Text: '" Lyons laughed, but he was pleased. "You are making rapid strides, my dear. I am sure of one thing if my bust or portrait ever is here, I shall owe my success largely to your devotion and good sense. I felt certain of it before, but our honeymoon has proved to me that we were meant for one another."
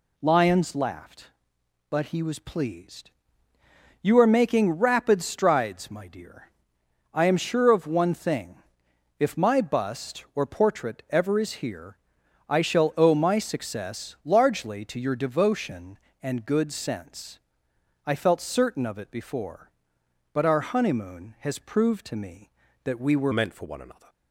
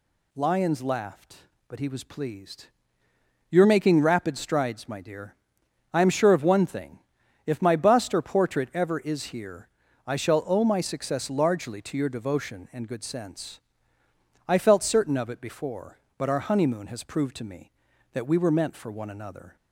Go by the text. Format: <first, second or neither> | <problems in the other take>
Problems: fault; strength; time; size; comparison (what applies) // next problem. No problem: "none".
second | pauses between "thing" and "if"; noticeable; at 8.5 s; 0.60 s long; noticeable in the second // changes voice at "meant"; from 23.3 s on; 0.7 s long